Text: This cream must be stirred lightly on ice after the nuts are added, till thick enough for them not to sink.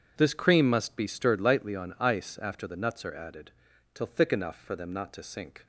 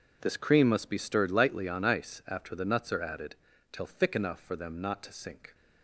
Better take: neither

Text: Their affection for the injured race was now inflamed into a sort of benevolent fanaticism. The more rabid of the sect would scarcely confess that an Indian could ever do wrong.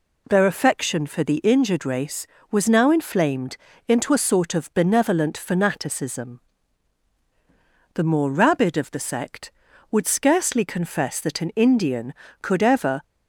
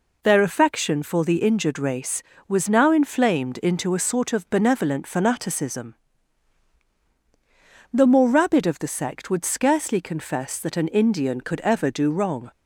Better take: second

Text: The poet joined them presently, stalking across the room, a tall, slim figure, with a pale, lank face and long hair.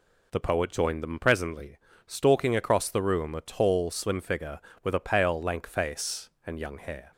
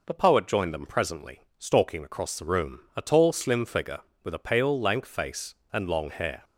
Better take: second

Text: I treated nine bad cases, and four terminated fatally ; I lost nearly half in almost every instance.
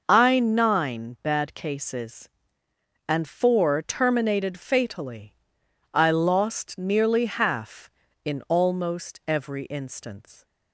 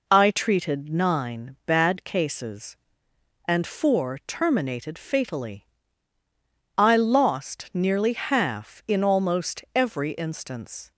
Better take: second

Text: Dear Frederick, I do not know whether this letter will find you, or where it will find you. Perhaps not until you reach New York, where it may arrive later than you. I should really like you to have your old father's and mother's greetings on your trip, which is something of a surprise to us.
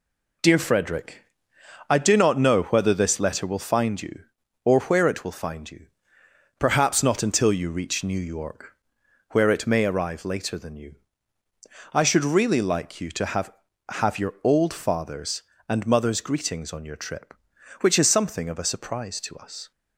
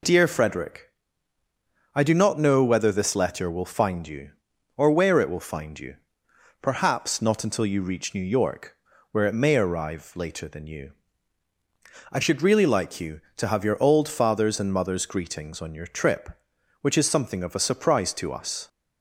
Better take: second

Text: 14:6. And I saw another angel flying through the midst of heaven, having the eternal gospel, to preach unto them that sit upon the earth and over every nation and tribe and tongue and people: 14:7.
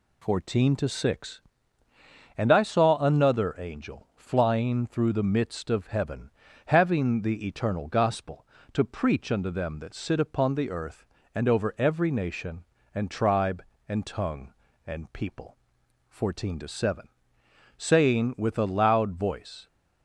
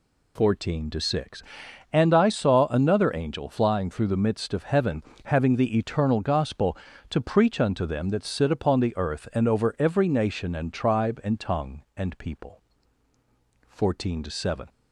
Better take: second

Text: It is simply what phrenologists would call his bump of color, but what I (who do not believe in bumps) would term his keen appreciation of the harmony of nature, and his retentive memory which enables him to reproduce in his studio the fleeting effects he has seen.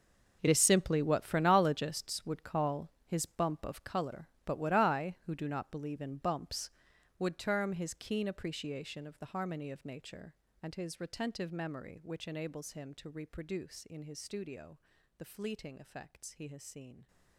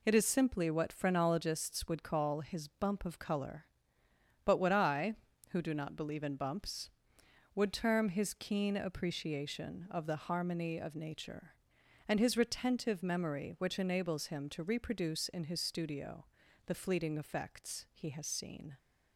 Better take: second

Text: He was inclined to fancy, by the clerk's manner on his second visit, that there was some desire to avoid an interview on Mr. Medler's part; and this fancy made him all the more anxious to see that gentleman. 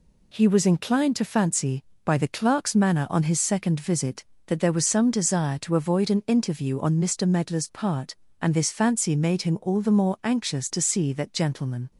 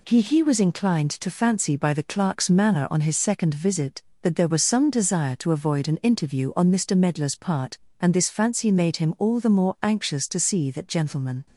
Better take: first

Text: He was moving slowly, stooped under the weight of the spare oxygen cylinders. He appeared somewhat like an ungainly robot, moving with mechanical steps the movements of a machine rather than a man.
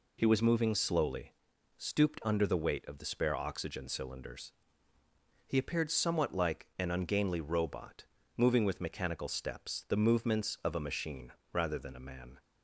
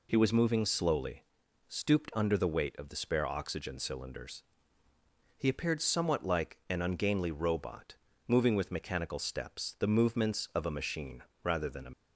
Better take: first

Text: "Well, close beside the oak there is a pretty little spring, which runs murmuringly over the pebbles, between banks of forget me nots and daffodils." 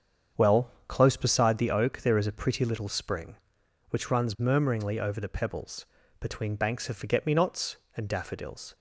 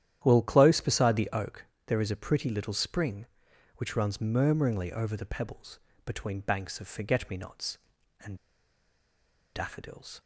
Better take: first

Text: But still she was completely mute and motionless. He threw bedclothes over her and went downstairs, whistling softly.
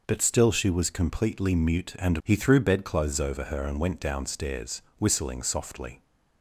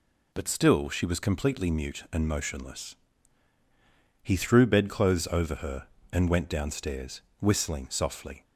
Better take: second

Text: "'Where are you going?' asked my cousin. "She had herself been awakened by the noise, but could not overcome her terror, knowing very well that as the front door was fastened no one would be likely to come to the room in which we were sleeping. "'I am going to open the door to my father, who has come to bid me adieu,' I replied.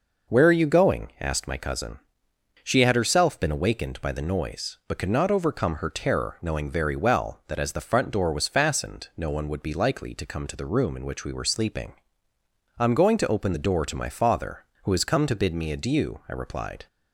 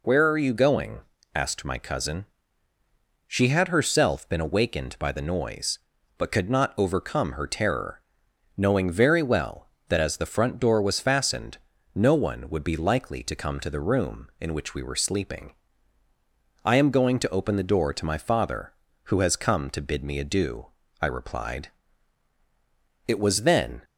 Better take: first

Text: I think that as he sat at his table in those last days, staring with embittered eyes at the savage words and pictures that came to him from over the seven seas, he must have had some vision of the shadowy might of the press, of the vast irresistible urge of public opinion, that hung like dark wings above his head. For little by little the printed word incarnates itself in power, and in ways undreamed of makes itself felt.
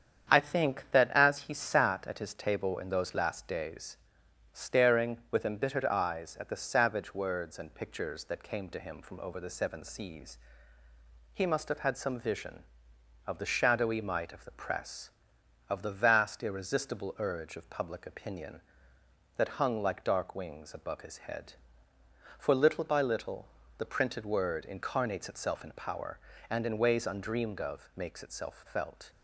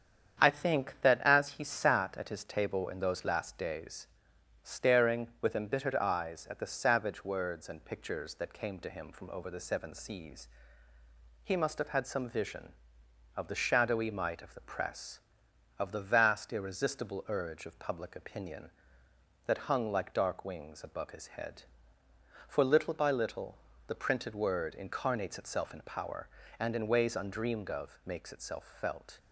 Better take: neither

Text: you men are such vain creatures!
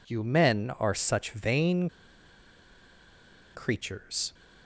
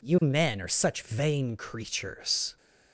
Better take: second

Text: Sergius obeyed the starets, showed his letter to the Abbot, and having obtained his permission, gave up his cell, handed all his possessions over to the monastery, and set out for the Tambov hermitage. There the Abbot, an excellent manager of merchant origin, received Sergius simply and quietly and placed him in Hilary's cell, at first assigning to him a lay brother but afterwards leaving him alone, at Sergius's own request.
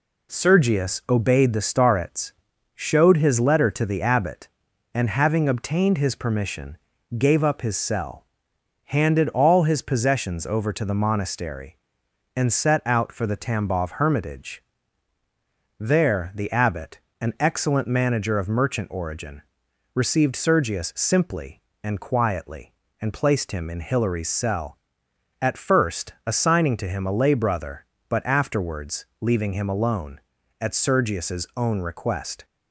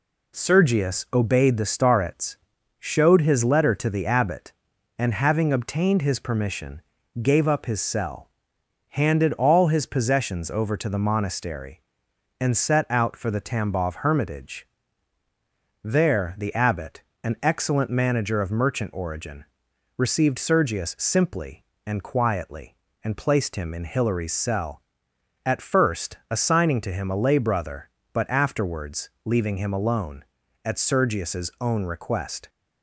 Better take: neither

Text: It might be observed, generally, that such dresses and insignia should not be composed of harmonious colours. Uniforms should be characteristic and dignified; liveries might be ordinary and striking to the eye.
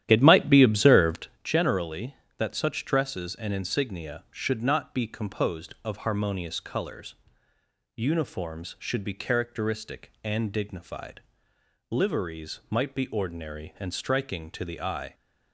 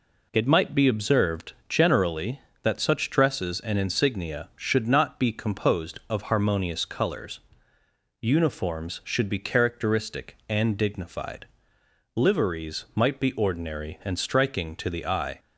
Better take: second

